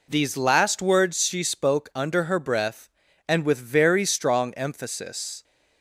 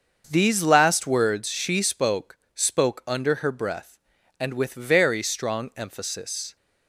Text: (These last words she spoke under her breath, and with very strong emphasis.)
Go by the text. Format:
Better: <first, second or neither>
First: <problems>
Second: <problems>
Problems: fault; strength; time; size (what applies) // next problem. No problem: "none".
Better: first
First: none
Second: starts louder than the rest; until 1.3 s; 6.5 dB // says "spoke" twice; at 2.5 s